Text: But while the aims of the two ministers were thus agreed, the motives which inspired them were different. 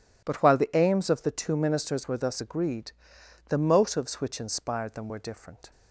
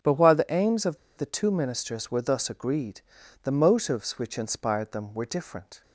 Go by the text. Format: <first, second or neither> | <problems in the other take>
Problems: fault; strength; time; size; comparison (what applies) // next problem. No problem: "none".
first | starts louder than the rest; strong; until 1.2 s; 8.5 dB // pauses between "of" and "the"; slight; at 0.9 s; 0.20 s long